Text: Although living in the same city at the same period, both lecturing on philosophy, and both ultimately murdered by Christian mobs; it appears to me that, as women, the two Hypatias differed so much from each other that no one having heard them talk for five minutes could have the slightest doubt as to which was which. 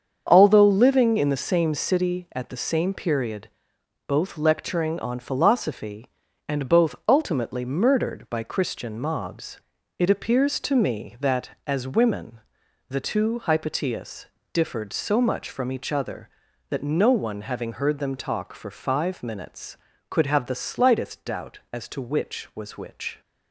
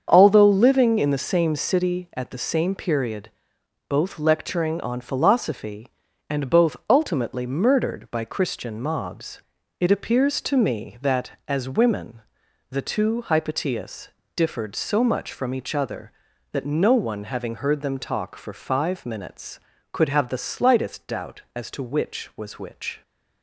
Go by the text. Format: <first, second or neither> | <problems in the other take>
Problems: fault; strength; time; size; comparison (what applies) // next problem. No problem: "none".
neither | starts louder than the rest; strong; the same in both // pauses between "Hypatias" and "differed"; slight; the same in both